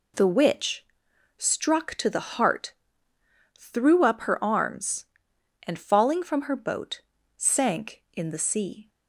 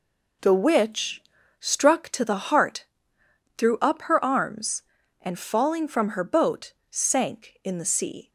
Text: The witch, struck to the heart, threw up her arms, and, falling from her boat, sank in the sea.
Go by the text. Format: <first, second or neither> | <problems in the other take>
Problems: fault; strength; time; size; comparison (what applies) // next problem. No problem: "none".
neither | none